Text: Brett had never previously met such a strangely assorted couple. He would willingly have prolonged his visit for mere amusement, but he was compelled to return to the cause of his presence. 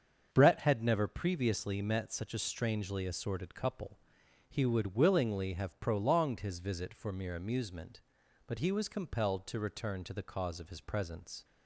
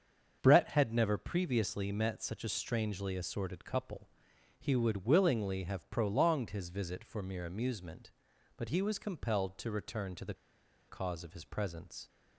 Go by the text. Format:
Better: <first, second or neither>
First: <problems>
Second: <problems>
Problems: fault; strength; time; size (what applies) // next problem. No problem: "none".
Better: first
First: starts louder than the rest; until 1.3 s; 7 dB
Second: starts louder than the rest; until 1.4 s; 7 dB // pauses between "the" and "cause"; noticeable; at 10.3 s; 0.55 s long